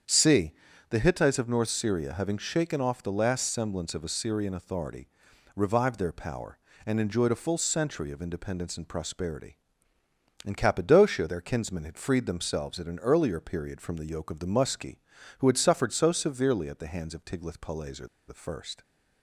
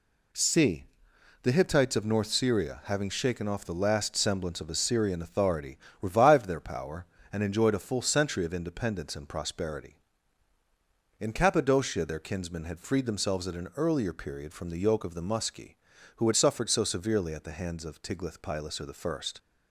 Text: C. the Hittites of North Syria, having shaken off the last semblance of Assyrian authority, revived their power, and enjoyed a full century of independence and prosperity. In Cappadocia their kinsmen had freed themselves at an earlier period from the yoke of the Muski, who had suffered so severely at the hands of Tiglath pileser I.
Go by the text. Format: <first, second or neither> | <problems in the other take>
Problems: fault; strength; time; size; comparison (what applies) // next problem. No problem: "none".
second | starts louder than the rest; strong; until 1.4 s; 8 dB // pauses between "pileser" and "I"; slight; at 18.0 s; 0.20 s long